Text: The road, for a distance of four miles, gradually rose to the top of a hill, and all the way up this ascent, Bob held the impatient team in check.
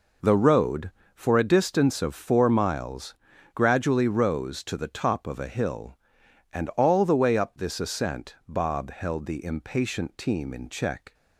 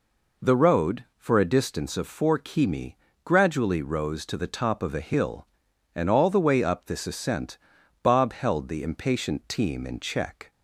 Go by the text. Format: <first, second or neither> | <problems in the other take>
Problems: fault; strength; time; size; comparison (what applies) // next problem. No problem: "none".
first | says "kimi" for "miles"; at 2.3 s